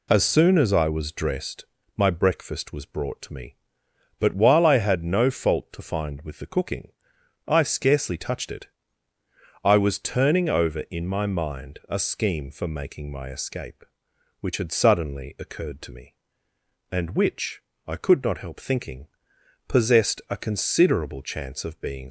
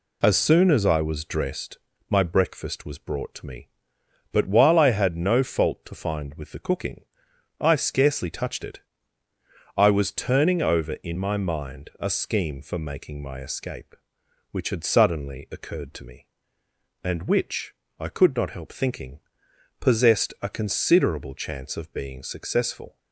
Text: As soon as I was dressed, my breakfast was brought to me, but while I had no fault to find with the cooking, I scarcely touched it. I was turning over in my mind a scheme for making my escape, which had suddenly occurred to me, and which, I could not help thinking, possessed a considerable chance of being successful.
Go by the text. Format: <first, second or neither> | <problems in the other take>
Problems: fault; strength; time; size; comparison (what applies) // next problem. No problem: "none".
second | stops before "successful"; at 22.0 s